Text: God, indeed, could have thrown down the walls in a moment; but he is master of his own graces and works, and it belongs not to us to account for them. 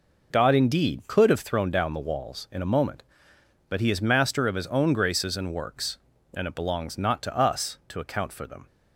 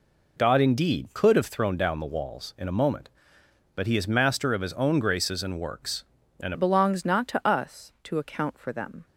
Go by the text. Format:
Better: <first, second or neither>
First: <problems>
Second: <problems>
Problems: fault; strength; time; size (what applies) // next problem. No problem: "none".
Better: first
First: none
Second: changes voice at "it"; from 6.5 s on; 2.5 s long